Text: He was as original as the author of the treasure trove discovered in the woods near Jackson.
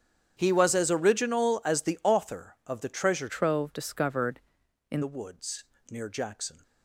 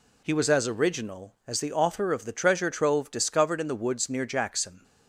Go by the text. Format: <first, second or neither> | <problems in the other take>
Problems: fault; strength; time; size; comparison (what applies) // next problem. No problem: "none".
second | starts louder than the rest; strong; until 1.3 s; 9 dB // changes voice from "trove" to "in"; from 3.2 to 5.0 s; 1.8 s long // pauses between "woods" and "near"; slight; at 5.6 s; 0.24 s long